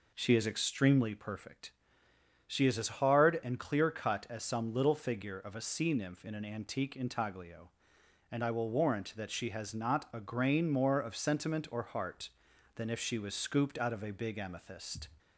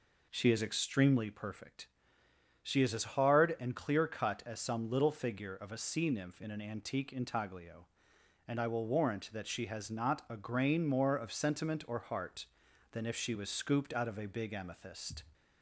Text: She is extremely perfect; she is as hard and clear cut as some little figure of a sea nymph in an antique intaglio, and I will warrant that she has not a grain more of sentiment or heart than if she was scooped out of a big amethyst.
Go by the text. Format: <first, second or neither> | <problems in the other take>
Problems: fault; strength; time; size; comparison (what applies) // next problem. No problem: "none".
neither | none